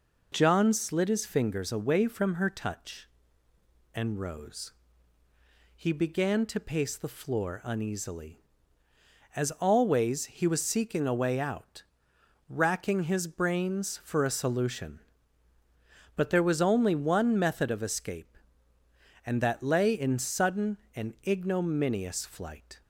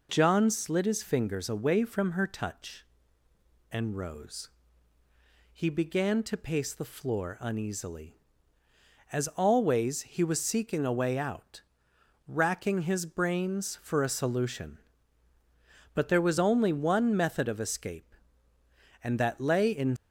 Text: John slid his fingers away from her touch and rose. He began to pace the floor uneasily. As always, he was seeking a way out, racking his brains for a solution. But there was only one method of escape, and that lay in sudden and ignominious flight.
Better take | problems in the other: first | stops before "sudden and ignominious flight"; at 19.9 s

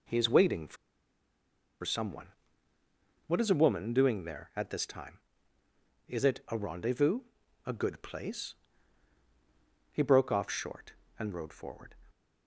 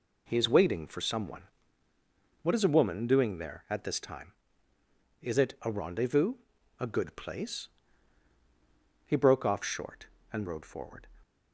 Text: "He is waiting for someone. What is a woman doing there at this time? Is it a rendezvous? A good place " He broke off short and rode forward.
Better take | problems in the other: second | pauses between "for" and "someone"; at 0.7 s; 1.0 s long

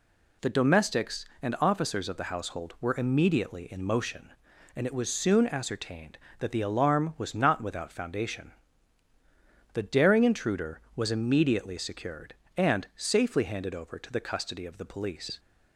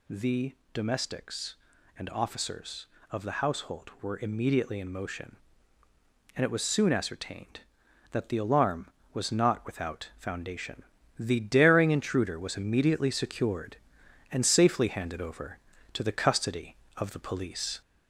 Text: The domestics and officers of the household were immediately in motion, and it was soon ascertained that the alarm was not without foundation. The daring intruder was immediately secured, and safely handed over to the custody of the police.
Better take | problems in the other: first | gets louder; slight; throughout; 2.5 dB // pauses between "The" and "domestics"; slight; at 0.5 s; 0.22 s long

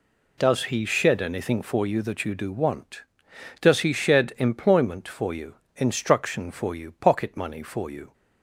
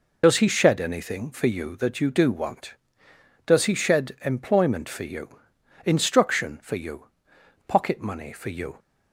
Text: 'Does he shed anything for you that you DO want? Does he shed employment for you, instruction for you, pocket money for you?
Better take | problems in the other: first | loses the start of "Does"; at 0.2 s; 50 ms

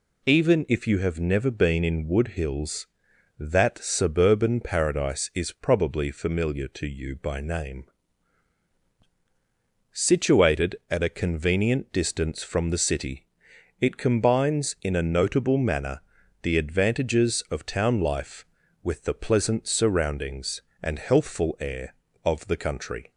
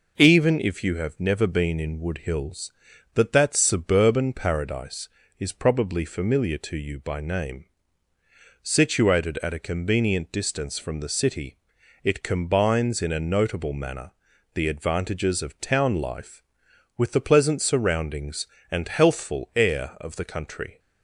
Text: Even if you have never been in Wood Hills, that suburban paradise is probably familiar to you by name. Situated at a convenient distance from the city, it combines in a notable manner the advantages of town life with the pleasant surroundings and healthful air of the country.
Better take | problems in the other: first | says "that" twice; at 3.3 s // pauses between "manner" and "the"; at 14.1 s; 0.42 s long; also in the first

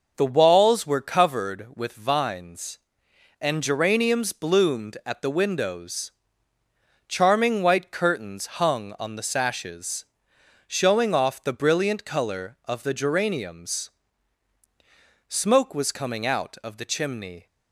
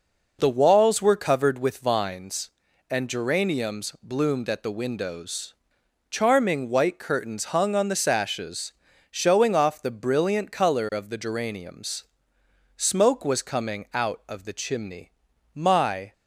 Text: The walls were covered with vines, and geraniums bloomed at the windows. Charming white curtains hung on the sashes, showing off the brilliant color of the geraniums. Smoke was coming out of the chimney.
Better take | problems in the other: first | goes on to say "My"; from 15.5 s on; 0.58 s long

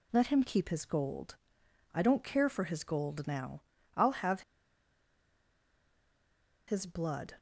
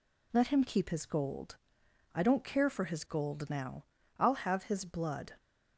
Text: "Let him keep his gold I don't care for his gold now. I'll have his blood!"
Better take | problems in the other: second | pauses between "gold" and "I"; noticeable; at 1.3 s; 0.58 s long; noticeable in the second // pauses between "have" and "his"; strong; at 4.3 s; 2.2 s long

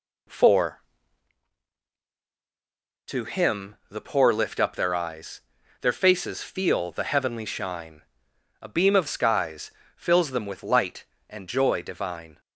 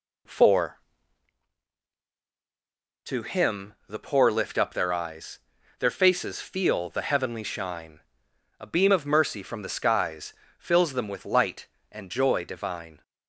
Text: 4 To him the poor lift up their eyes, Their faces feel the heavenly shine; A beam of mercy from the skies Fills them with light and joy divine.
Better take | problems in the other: second | skips "mercy from the"; at 9.0 s // pauses between "skies" and "Fills"; slight; at 9.6 s; 0.26 s long; slight in the second

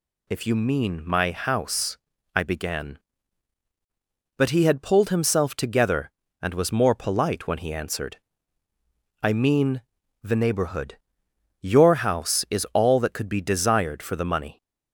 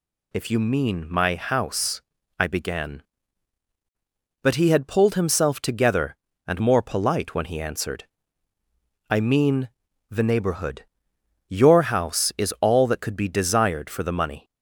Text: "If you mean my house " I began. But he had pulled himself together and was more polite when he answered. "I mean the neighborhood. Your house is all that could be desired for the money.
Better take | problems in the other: first | skips "was"; at 6.5 s // pauses between "mean" and "the"; at 9.6 s; 0.40 s long; also in the first

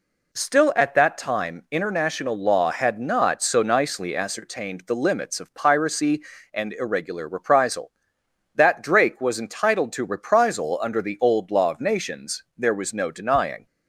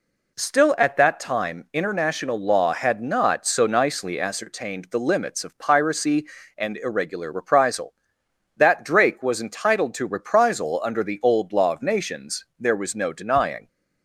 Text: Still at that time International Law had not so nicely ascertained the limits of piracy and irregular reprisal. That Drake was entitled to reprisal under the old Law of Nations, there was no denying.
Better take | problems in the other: neither | none

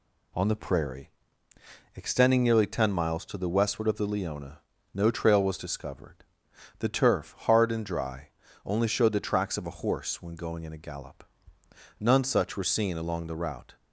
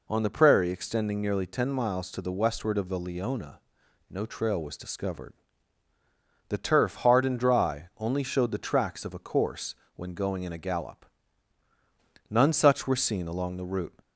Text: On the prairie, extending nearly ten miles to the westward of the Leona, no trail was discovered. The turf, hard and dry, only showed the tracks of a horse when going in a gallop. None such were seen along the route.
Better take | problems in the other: first | says "course" for "horse"; at 9.1 s

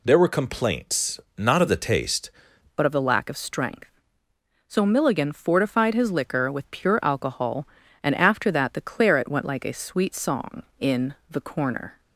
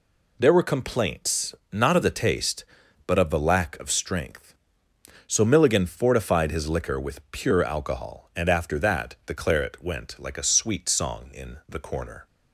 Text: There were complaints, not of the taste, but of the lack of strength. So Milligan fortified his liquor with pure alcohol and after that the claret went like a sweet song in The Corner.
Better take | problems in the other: second | changes voice at "but"; from 2.7 s on; 9.2 s long // pauses between "in" and "The"; slight; at 11.1 s; 0.16 s long

